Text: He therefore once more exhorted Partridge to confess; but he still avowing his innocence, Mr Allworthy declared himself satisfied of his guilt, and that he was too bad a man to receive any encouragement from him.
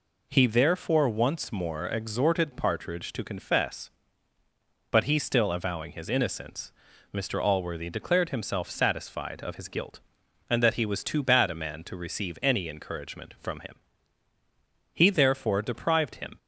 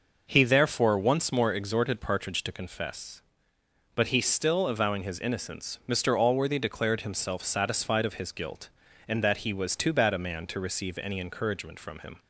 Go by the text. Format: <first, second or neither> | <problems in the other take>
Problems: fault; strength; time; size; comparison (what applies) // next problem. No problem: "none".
second | goes on to say "He therefore deprived him"; from 14.9 s on; 1.4 s long